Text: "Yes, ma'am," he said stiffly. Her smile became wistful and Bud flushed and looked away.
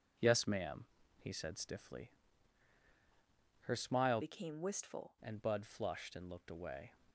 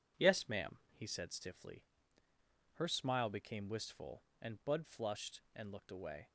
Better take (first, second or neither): second